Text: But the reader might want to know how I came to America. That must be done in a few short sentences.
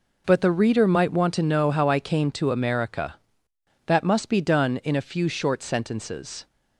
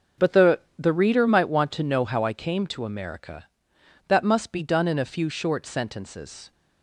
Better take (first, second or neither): first